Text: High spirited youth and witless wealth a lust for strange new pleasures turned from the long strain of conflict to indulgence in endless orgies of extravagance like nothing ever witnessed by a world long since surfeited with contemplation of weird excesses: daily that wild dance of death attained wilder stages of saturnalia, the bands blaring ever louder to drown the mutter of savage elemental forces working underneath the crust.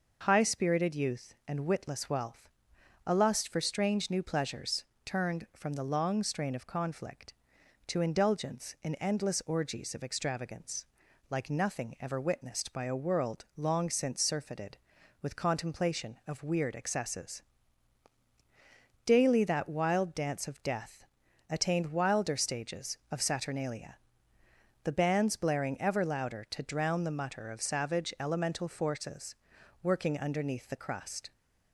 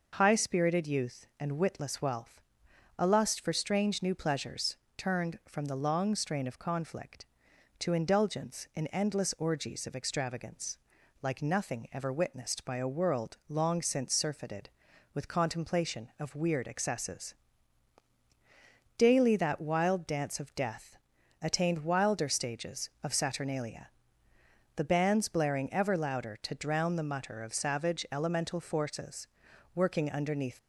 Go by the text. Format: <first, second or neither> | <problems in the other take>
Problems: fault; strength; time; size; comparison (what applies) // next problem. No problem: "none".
first | pauses between "wealth" and "a"; noticeable; at 2.3 s; 0.60 s long; noticeable in the first // pauses between "pleasures" and "turned"; slight; at 4.7 s; 0.20 s long; slight in the first // pauses between "extravagance" and "like"; noticeable; at 10.7 s; 0.46 s long; noticeable in the first // pauses between "death" and "attained"; noticeable; at 20.9 s; 0.46 s long; noticeable in the first // pauses between "forces" and "working"; noticeable; at 29.2 s; 0.50 s long; noticeable in the first // stops before "the crust"; at 30.5 s